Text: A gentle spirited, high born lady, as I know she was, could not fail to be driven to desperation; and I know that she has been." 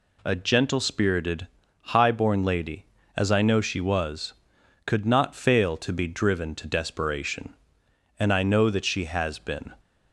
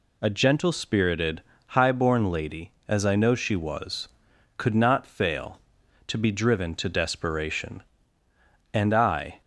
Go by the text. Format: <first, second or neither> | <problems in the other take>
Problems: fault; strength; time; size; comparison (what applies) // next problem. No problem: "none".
first | stops before "know that she has been"; at 9.4 s